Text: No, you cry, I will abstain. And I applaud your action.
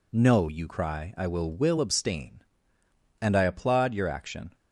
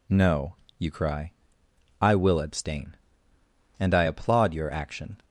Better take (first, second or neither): second